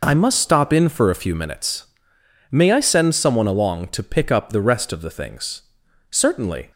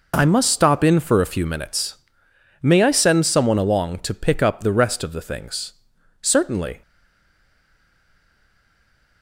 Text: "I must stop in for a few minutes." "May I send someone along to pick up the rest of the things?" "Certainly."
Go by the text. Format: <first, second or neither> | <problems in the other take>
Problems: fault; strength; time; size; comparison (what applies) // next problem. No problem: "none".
first | stays silent after the last word; from 6.8 s on; 2.4 s long